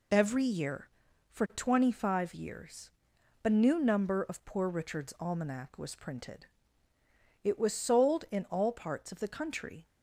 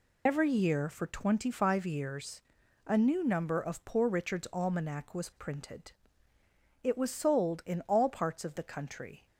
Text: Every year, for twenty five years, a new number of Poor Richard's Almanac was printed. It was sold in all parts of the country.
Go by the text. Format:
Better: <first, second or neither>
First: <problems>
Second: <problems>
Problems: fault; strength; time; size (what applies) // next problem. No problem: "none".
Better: first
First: none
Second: loses the start of "Every"; at 0.2 s; 60 ms